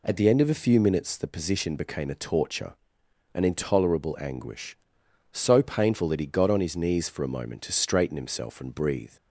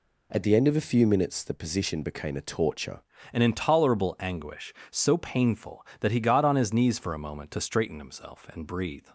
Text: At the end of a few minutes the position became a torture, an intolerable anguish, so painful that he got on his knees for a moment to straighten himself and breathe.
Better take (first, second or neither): first